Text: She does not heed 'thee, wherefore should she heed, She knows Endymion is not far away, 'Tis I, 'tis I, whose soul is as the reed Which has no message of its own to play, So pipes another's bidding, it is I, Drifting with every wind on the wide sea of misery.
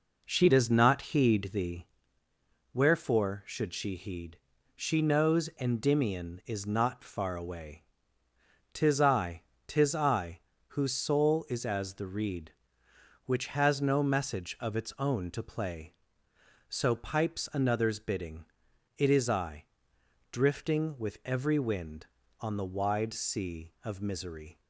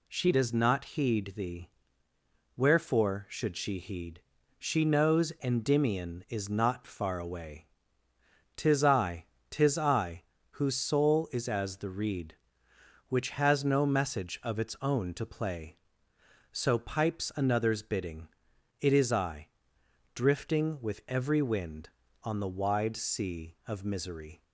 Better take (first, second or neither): second